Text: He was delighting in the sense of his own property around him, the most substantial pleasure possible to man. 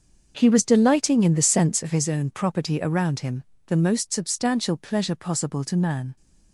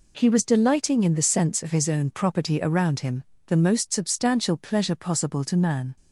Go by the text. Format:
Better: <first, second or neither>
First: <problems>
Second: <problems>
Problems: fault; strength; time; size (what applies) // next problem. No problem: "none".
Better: second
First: starts louder than the rest; until 2.1 s; 6.5 dB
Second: none